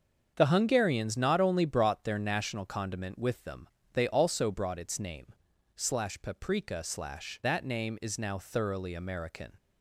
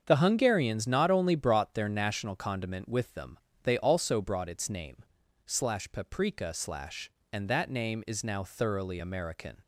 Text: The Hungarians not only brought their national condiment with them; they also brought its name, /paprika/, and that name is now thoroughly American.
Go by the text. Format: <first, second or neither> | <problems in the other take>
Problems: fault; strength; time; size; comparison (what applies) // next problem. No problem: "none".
second | starts louder than the rest; until 1.3 s; 7 dB; also in the second // skips "and"; at 7.4 s